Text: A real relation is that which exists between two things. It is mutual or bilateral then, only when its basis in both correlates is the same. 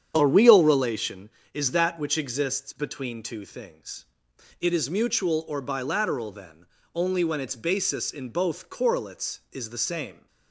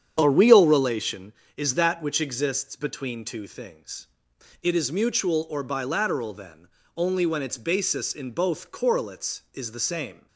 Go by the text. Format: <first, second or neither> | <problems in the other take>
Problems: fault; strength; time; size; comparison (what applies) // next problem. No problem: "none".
neither | starts louder than the rest; strong; the same in both